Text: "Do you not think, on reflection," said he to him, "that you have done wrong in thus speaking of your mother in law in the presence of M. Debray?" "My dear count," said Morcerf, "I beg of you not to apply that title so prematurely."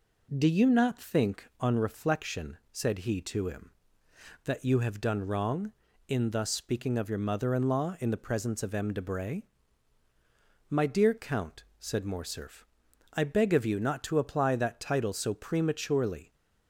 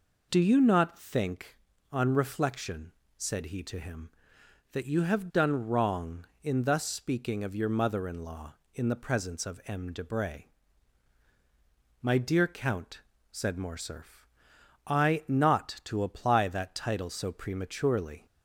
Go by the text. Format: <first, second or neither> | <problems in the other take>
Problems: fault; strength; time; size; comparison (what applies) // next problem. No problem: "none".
first | skips "beg of you"; at 15.2 s